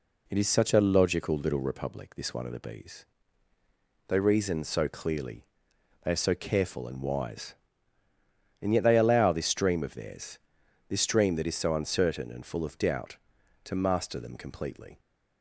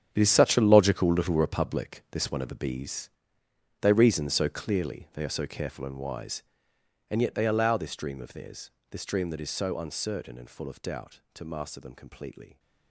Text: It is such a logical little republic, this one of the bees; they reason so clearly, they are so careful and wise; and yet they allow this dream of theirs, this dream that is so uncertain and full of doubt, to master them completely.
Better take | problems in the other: first | gets quieter; strong; throughout; 13.5 dB

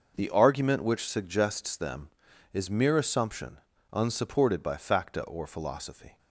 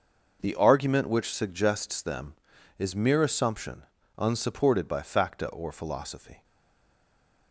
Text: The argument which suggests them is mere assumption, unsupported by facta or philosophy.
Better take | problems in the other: first | stays silent after the last word; from 6.4 s on; 1.1 s long

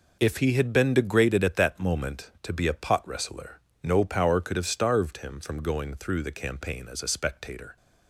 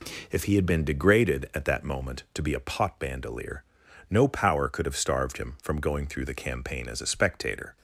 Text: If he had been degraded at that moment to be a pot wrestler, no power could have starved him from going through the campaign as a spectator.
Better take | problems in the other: first | says "bandolier" for "wrestler"; at 2.9 s

